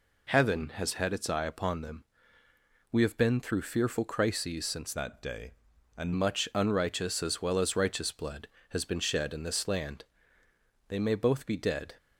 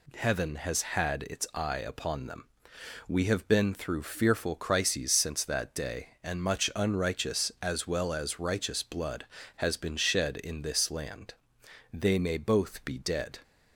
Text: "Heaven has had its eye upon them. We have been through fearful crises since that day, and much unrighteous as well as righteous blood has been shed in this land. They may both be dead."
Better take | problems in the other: second | changes voice from "that" to "and"; from 4.9 to 6.1 s; 1.2 s long

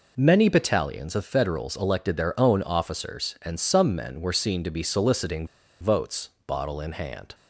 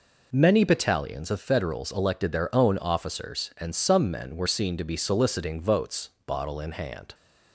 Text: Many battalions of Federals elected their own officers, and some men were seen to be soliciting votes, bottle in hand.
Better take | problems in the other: second | pauses between "soliciting" and "votes"; slight; at 5.4 s; 0.35 s long

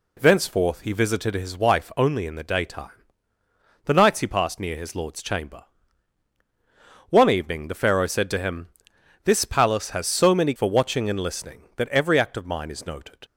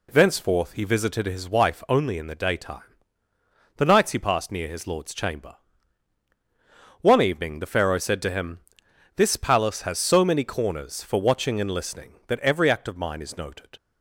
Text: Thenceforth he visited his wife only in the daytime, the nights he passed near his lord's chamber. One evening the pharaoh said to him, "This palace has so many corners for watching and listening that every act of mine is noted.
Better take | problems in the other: second | skips "corners"; at 10.5 s

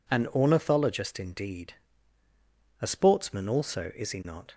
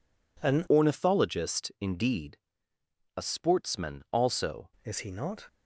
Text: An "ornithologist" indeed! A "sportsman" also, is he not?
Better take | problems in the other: first | changes voice from "ornithologist" to "also"; from 0.6 to 4.7 s; 4.1 s long

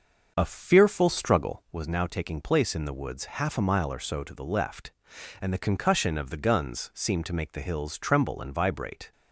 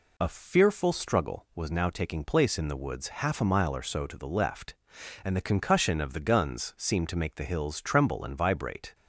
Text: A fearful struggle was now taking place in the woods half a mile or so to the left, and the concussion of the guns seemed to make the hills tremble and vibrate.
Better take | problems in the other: second | starts louder than the rest; until 1.8 s; 6.5 dB

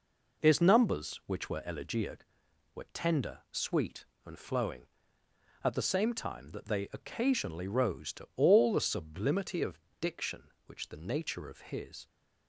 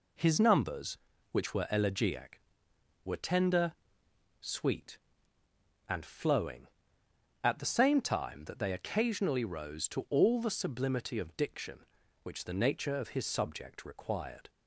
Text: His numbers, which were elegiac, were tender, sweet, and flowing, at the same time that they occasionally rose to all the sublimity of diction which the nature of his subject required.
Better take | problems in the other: second | pauses between "of" and "diction"; slight; at 9.7 s; 0.22 s long // stops before "subject required"; at 12.0 s

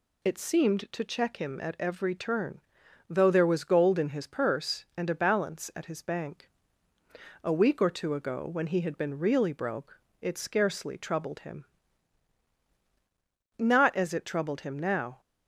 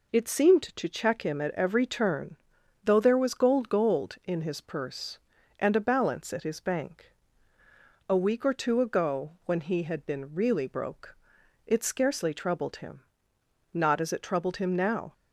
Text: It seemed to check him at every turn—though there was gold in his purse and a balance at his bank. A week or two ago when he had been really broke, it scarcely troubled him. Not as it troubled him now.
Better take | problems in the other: first | says "gold" twice; at 3.6 s

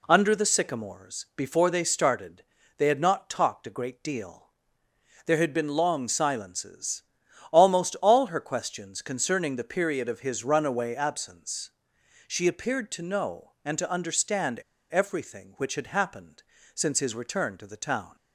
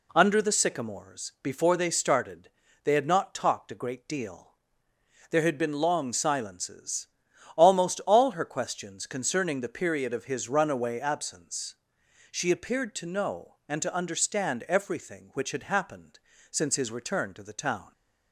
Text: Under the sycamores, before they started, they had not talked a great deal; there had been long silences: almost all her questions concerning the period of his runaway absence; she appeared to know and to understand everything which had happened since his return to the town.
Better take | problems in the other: second | pauses between "understand" and "everything"; slight; at 14.5 s; 0.30 s long // pauses between "happened" and "since"; slight; at 16.4 s; 0.30 s long; slight in the second

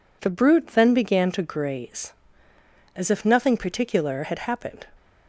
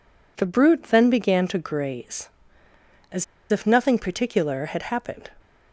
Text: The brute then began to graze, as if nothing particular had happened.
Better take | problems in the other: first | pauses between "as" and "if"; slight; at 3.2 s; 0.25 s long

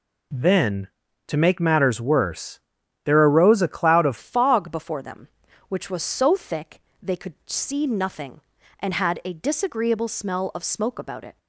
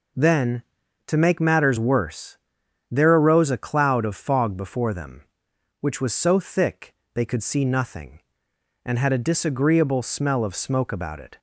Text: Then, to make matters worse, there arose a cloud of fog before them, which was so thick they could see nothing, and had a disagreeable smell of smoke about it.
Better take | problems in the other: second | changes voice at "fog"; from 4.1 s on; 7.2 s long // pauses between "thick" and "they"; slight; at 6.7 s; 0.22 s long; slight in the second

